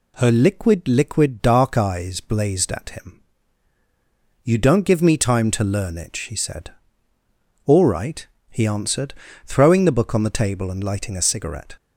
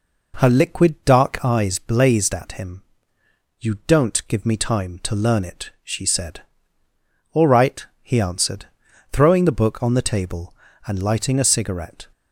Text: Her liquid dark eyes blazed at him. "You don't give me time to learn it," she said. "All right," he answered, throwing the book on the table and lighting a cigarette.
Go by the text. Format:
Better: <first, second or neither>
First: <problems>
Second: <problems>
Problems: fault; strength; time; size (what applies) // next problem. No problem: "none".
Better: second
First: says "liquid" twice; at 0.8 s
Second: none